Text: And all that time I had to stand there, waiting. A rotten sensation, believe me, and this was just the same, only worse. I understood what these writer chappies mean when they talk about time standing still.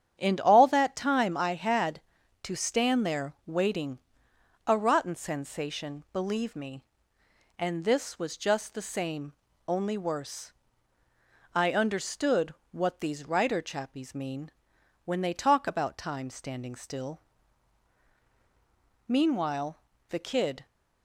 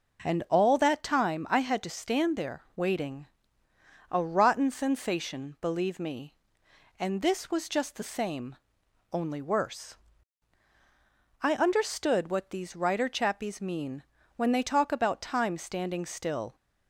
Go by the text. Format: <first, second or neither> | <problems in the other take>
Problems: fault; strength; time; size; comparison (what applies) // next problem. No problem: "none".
second | starts louder than the rest; strong; until 1.2 s; 9 dB // pauses between "understood" and "what"; slight; at 12.5 s; 0.18 s long // pauses between "mean" and "when"; noticeable; at 14.5 s; 0.54 s long; slight in the second // goes on to say "Meanwhile the kid"; from 19.0 s on; 1.5 s long